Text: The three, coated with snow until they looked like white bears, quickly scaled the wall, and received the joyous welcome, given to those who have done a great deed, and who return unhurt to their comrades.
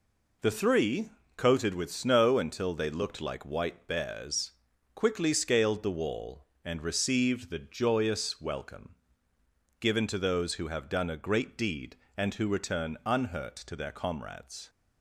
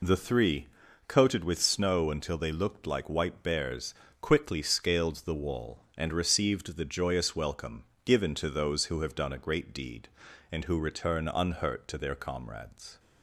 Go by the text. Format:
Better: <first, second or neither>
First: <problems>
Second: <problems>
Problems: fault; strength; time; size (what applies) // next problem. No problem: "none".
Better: neither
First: none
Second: none